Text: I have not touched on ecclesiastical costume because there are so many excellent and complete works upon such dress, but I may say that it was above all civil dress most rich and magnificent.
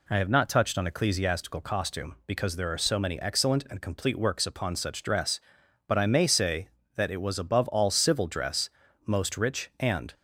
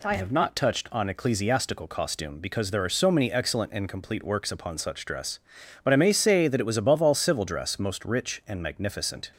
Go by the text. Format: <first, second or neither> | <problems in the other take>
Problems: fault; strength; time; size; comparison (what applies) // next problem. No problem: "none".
second | pauses between "dress" and "most"; slight; at 8.6 s; 0.36 s long // stops before "magnificent"; at 10.1 s